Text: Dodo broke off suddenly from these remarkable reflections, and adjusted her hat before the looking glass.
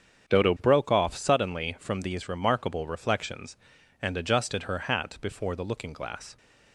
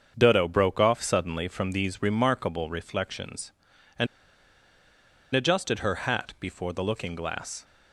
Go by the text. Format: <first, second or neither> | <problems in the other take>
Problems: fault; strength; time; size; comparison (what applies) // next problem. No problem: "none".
first | starts louder than the rest; strong; until 1.1 s; 7 dB; strong in the first // pauses between "and" and "adjusted"; strong; at 4.0 s; 1.2 s long